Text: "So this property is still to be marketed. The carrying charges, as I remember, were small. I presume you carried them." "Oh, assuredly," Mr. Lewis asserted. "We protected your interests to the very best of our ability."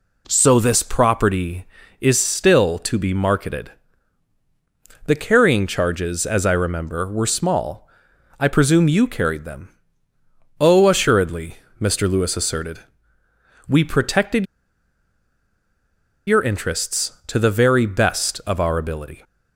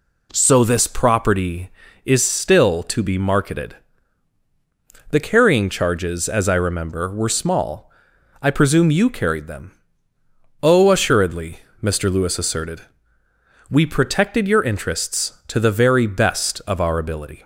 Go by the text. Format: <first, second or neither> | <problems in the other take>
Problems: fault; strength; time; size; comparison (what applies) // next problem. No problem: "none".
second | pauses between "protected" and "your"; strong; at 14.4 s; 1.8 s long